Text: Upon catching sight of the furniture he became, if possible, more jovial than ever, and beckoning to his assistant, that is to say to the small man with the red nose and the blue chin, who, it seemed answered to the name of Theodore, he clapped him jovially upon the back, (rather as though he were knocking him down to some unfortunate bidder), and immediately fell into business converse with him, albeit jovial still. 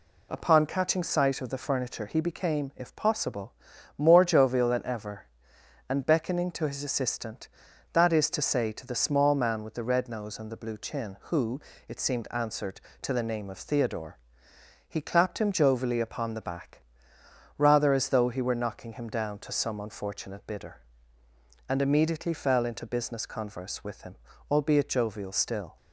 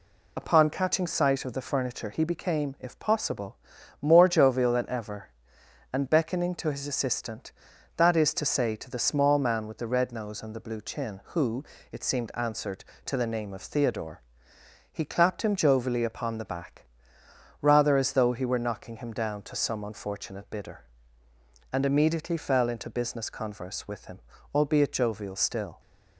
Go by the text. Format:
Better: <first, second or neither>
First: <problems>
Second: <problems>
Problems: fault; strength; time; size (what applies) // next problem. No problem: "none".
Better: first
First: none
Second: loses the start of "Upon"; at 0.3 s; 30 ms